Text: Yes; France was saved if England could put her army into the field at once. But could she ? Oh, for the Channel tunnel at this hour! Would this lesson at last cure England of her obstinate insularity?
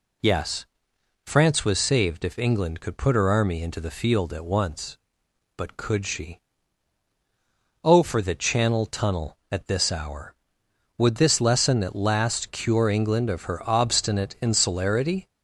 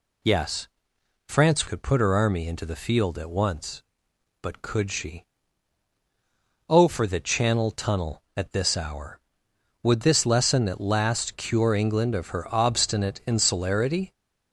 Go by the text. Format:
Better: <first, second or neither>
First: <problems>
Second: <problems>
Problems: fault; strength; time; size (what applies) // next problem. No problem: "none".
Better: first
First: none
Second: skips "was saved if England"; at 1.6 s